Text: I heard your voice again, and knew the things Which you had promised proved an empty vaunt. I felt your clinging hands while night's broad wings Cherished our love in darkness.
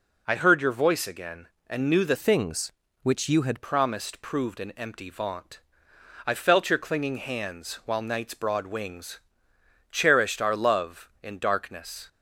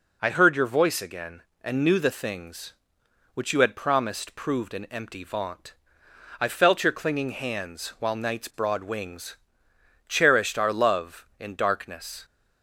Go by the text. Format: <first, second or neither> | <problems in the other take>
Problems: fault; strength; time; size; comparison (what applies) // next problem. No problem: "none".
second | changes voice from "things" to "had"; from 2.1 to 3.6 s; 1.5 s long // pauses between "wings" and "Cherished"; noticeable; at 9.1 s; 0.72 s long; noticeable in the second